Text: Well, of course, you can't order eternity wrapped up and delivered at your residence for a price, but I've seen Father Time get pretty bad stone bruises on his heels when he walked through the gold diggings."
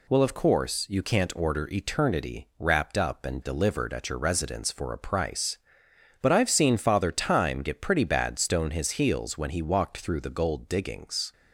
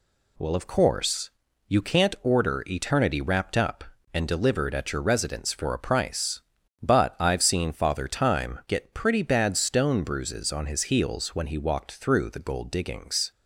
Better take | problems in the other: second | skips "bruises on"; at 8.7 s

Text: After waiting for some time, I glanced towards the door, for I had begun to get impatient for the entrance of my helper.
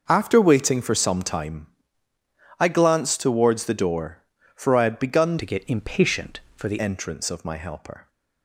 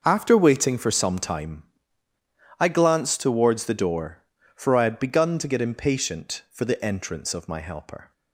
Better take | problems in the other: second | starts louder than the rest; until 1.0 s; 6 dB; also in the second // changes voice from "to" to "the"; from 5.3 to 6.8 s; 1.5 s long

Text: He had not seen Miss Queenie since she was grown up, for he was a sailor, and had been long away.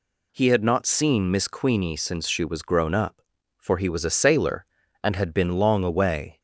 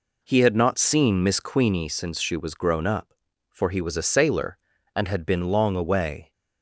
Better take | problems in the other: first | starts louder than the rest; slight; until 2.0 s; 3.5 dB

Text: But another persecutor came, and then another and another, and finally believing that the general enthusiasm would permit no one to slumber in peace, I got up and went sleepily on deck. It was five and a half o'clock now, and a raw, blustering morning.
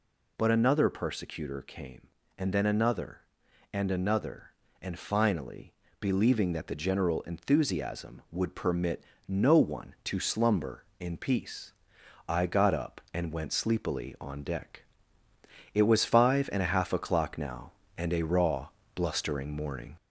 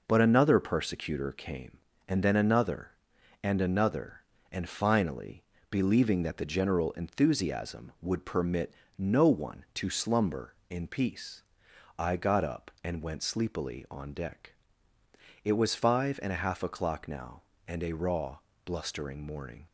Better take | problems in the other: second | gets louder; slight; throughout; 2 dB // pauses between "finally" and "believing"; slight; at 5.7 s; 0.28 s long; slight in the second // pauses between "permit" and "no"; slight; at 9.0 s; 0.24 s long; slight in the second

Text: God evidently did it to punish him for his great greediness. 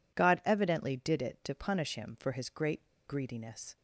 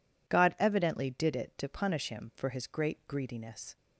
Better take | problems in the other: second | pauses between "great" and "greediness"; slight; at 2.8 s; 0.18 s long

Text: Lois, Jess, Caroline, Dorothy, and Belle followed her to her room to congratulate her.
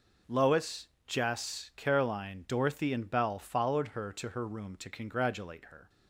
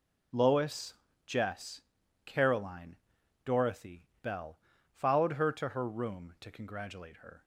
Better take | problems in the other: first | skips "and"; at 4.1 s // pauses between "Belle" and "followed"; slight; at 4.5 s; 0.32 s long

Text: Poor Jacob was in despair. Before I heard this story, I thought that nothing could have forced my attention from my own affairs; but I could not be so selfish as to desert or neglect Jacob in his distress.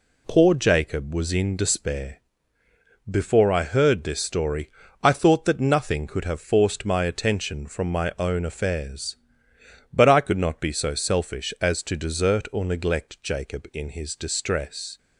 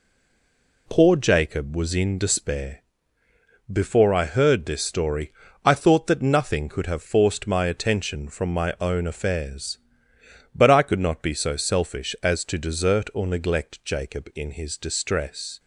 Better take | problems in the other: first | stays silent before the first word; slight; until 0.8 s; 0.8 s long

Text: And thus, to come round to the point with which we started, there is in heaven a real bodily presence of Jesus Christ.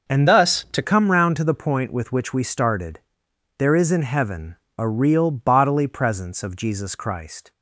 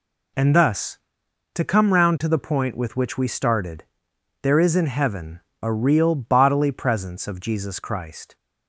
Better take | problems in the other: second | starts louder than the rest; until 1.1 s; 6 dB // changes voice from "thus" to "to"; from 0.2 to 0.8 s; 0.6 s long // pauses between "heaven" and "a"; slight; at 4.5 s; 0.22 s long; slight in the second

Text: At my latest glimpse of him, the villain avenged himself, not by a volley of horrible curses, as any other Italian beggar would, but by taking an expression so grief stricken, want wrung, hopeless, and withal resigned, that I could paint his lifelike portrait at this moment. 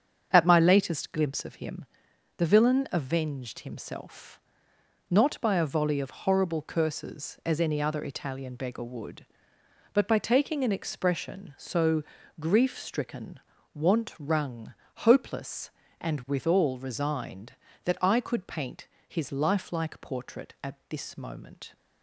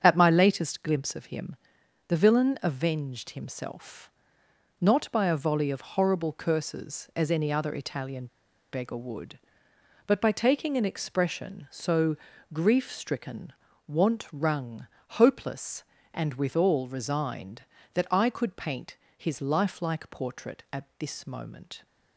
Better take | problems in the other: first | starts louder than the rest; until 1.0 s; 7 dB; strong in the first // pauses between "Italian" and "beggar"; at 8.2 s; 0.45 s long // pauses between "so" and "grief"; at 12.1 s; 0.38 s long; also in the first // pauses between "paint" and "his"; slight; at 18.9 s; 0.20 s long; slight in the first

